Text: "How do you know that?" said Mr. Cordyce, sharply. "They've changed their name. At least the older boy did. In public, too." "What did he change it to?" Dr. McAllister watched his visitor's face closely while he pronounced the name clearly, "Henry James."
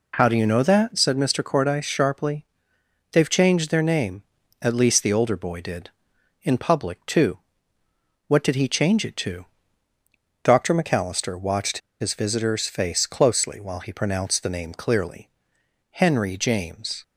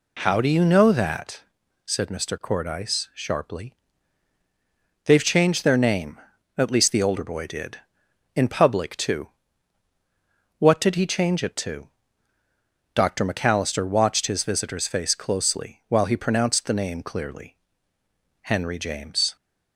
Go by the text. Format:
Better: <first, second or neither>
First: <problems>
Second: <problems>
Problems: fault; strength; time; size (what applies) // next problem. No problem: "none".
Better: second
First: pauses between "watched" and "his"; slight; at 11.7 s; 0.22 s long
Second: none